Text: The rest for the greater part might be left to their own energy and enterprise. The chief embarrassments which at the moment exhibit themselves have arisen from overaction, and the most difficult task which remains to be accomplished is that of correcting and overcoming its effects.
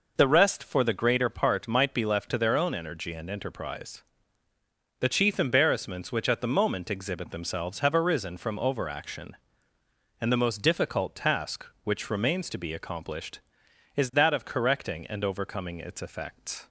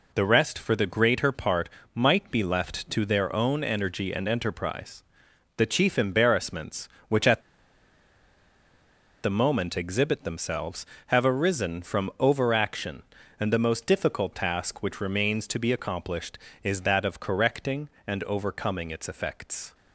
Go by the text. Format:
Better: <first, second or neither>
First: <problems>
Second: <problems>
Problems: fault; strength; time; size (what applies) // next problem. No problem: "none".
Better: first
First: none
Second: pauses between "part" and "might"; slight; at 1.6 s; 0.26 s long // pauses between "at" and "the"; strong; at 7.4 s; 1.8 s long